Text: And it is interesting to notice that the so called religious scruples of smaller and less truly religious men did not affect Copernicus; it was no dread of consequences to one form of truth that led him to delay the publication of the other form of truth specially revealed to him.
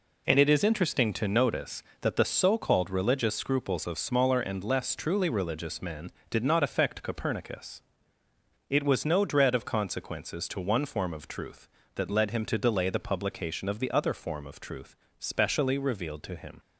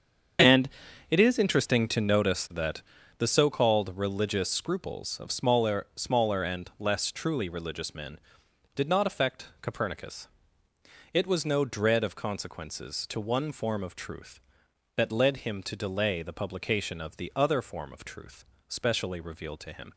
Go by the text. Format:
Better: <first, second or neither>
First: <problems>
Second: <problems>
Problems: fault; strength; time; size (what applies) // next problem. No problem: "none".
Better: first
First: pauses between "truth" and "specially"; slight; at 14.9 s; 0.22 s long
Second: starts louder than the rest; strong; until 1.8 s; 7.5 dB // pauses between "And" and "it"; at 0.7 s; 0.40 s long // pauses between "that" and "the"; at 2.8 s; 0.38 s long // says "smaller" twice; at 5.9 s // pauses between "truth" and "specially"; slight; at 18.4 s; 0.24 s long